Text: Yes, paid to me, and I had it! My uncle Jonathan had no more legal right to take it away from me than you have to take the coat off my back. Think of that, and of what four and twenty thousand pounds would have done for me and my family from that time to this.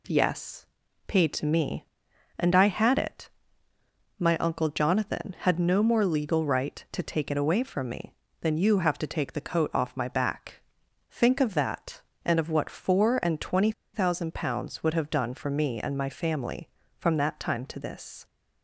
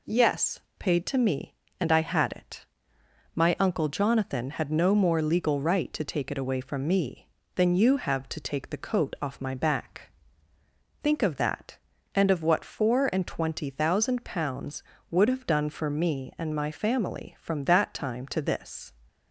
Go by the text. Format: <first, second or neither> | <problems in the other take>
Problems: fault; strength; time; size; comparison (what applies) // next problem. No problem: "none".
second | pauses between "twenty" and "thousand"; slight; at 13.7 s; 0.22 s long